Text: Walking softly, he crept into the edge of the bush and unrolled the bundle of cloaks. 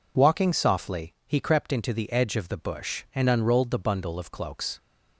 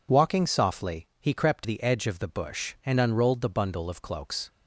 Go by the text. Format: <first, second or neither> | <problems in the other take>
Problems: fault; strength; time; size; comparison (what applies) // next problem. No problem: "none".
first | skips "into"; at 1.6 s